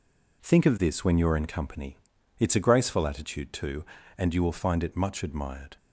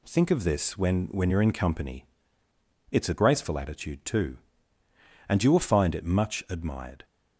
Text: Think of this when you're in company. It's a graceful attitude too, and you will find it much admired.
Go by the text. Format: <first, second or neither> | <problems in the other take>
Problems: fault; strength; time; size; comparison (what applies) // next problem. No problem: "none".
first | says "when" twice; at 1.1 s